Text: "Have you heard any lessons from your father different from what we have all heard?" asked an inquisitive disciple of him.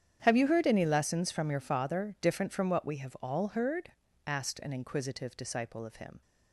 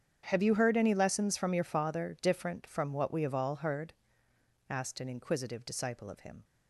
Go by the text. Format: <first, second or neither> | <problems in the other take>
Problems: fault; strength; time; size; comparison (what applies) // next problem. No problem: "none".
neither | starts louder than the rest; strong; the same in both